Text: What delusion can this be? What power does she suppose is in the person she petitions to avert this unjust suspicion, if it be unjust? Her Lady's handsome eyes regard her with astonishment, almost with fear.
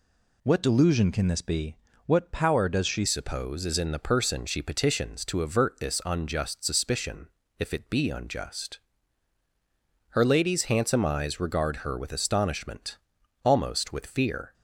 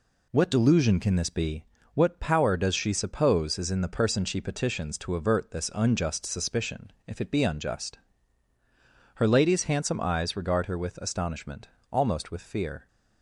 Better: second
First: changes voice at "suppose"; from 3.0 s on; 11.5 s long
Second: none

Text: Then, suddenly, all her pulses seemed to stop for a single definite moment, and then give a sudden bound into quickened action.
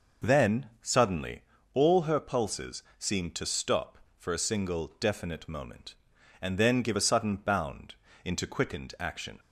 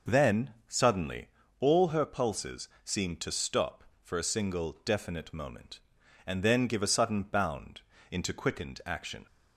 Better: neither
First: pauses between "pulses" and "seemed"; slight; at 2.8 s; 0.16 s long // pauses between "bound" and "into"; slight; at 7.9 s; 0.32 s long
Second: pauses between "pulses" and "seemed"; slight; at 2.6 s; 0.16 s long // pauses between "bound" and "into"; slight; at 7.7 s; 0.32 s long

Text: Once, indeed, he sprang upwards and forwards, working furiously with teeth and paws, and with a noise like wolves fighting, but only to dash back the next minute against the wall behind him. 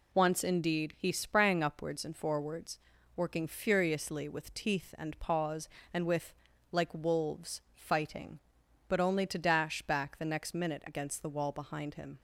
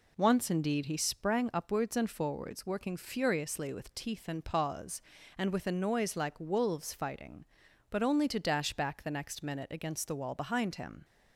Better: second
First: skips "a noise"; at 6.5 s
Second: none

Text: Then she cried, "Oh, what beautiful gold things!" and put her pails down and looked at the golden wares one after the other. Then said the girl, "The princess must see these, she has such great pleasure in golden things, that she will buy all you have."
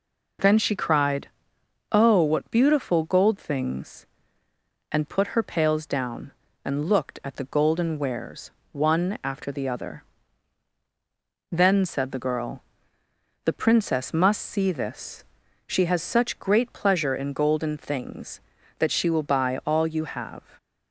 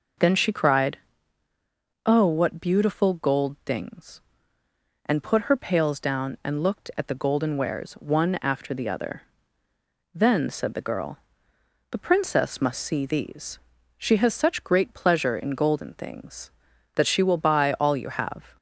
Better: second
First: pauses between "wares" and "one"; slight; at 8.5 s; 0.22 s long // says "this" for "these"; at 14.7 s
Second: none

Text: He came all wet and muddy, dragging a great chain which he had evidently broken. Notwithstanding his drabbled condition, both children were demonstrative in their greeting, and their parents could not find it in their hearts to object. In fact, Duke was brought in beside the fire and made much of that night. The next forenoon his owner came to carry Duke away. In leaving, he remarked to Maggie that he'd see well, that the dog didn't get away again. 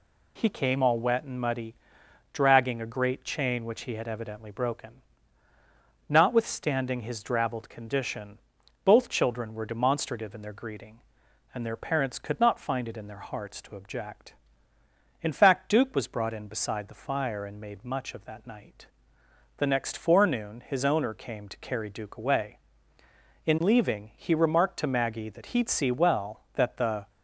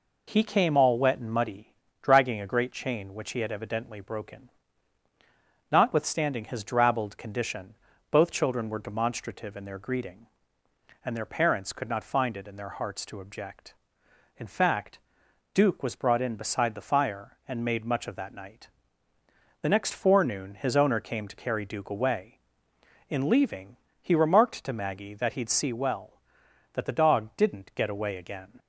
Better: second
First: stops before "dog didn't get away again"; at 27.0 s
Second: none

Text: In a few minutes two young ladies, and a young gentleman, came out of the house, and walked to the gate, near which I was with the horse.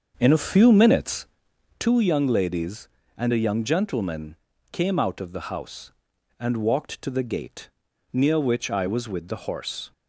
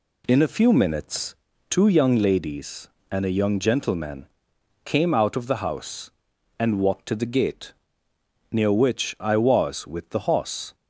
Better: second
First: starts louder than the rest; until 1.9 s; 6.5 dB // pauses between "minutes" and "two"; noticeable; at 1.2 s; 0.52 s long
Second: pauses between "minutes" and "two"; slight; at 1.3 s; 0.34 s long

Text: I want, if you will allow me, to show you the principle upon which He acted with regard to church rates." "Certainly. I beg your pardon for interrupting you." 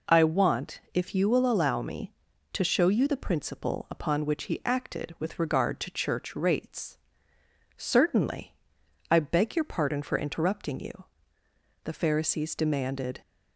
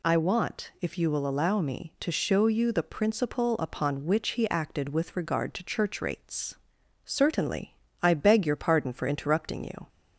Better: second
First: goes on to say "The Pharisees demanded"; from 11.8 s on; 1.3 s long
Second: none

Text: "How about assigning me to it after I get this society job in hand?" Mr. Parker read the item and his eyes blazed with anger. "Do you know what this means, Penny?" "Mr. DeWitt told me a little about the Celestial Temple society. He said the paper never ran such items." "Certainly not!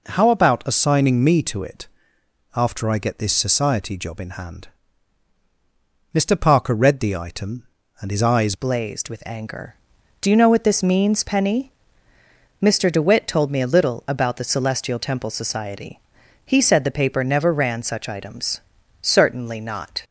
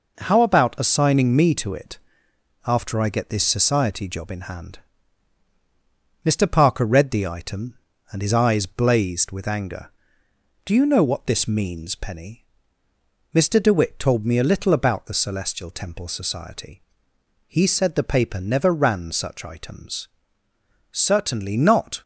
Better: second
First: pauses between "it" and "after"; noticeable; at 1.8 s; 0.68 s long // changes voice at "blazed"; from 8.5 s on; 11.5 s long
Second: pauses between "it" and "after"; noticeable; at 1.9 s; 0.68 s long

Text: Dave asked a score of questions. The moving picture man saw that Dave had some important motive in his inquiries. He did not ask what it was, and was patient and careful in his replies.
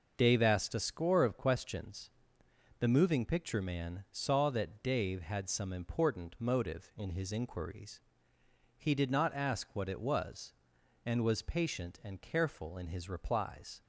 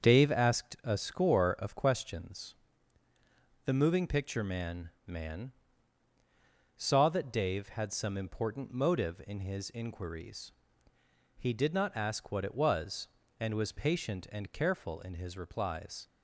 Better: first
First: none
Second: starts louder than the rest; until 1.0 s; 7 dB // says "man" twice; at 5.0 s

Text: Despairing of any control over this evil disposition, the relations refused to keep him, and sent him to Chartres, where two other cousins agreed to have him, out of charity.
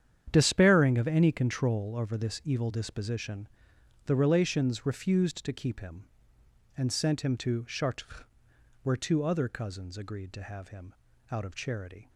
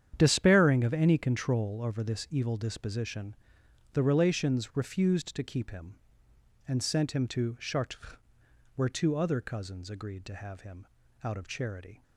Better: neither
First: starts louder than the rest; strong; until 1.3 s; 9 dB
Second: starts louder than the rest; strong; until 1.1 s; 9 dB

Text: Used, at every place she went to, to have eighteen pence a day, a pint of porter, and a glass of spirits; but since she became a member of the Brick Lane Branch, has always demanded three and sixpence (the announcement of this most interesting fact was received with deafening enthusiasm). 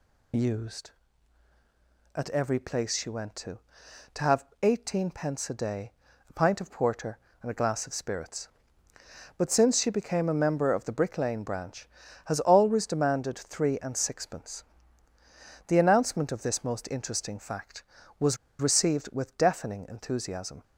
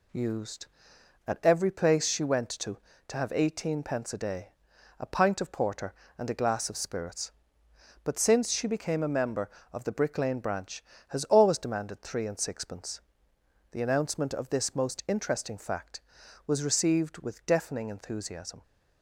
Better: second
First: pauses between "have" and "eighteen"; slight; at 4.4 s; 0.18 s long // pauses between "was" and "received"; slight; at 18.3 s; 0.22 s long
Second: none

